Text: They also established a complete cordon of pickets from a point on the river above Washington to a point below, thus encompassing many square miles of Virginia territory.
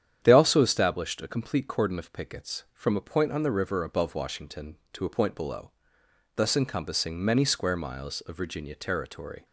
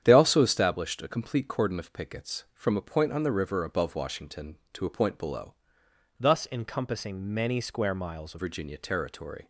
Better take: first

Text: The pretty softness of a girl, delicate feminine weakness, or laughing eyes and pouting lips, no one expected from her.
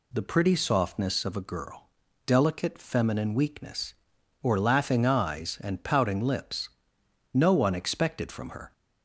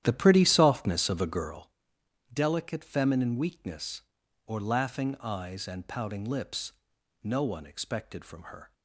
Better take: first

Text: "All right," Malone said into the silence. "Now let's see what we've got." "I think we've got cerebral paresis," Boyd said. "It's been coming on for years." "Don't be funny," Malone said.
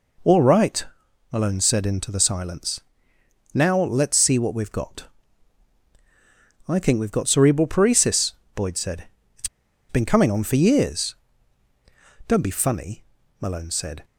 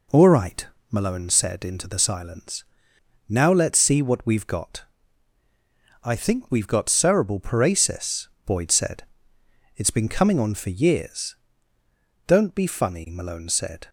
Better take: second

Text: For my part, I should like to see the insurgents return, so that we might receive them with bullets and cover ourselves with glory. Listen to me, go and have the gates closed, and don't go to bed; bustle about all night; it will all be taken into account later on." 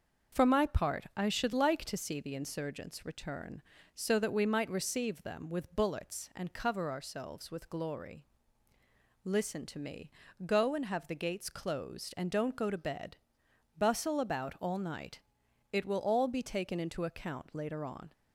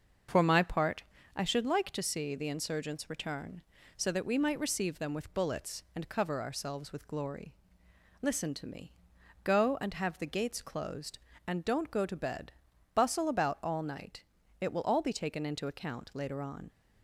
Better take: neither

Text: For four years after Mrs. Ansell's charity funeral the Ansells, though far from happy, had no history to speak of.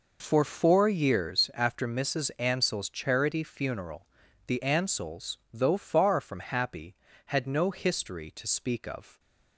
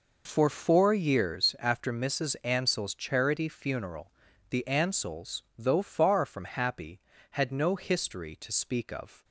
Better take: neither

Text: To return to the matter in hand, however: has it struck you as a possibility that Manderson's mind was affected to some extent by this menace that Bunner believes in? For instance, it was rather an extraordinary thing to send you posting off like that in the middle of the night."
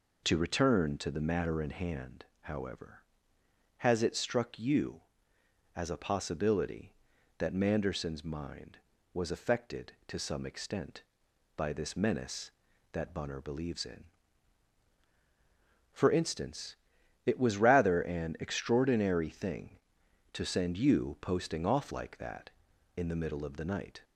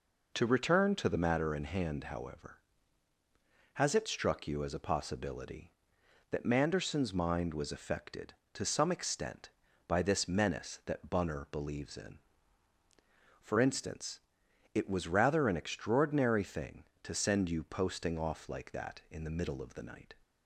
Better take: neither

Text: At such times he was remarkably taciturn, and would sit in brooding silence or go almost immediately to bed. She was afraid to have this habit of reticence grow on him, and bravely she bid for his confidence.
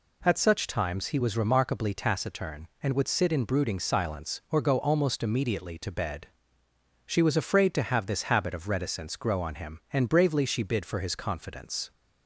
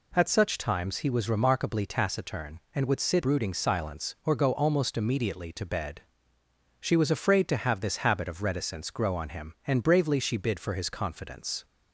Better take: first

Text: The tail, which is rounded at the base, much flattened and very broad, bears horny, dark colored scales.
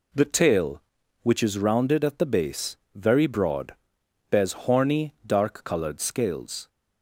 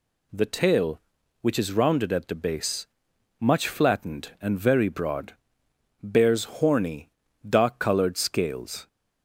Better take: second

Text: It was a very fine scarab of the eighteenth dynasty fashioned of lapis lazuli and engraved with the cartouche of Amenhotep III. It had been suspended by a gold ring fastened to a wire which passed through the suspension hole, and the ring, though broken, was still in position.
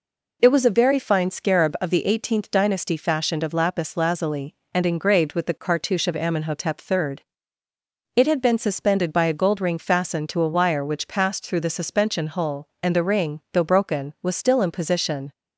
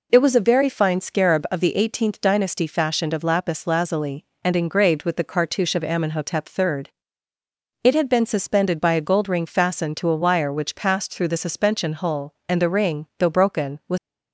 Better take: first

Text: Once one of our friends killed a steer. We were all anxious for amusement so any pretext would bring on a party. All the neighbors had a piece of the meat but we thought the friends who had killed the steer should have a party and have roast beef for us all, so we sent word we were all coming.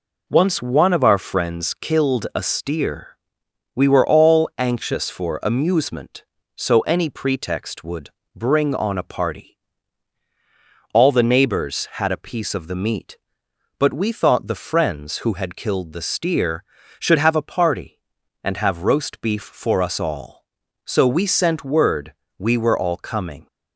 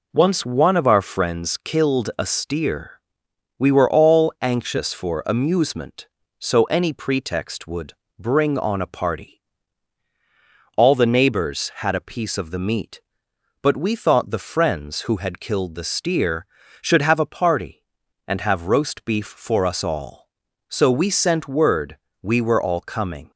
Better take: neither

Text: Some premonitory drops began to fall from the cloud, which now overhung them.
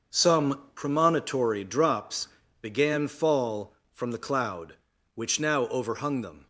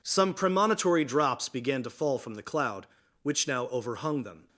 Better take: second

